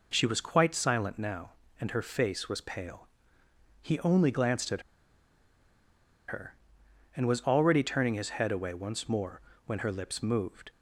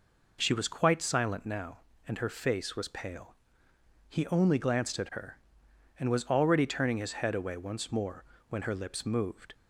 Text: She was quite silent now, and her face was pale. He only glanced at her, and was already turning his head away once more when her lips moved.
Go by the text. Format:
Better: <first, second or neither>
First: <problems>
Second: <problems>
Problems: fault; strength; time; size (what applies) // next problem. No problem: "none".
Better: second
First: pauses between "at" and "her"; strong; at 4.8 s; 1.4 s long // pauses between "more" and "when"; slight; at 9.4 s; 0.26 s long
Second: pauses between "more" and "when"; slight; at 8.2 s; 0.26 s long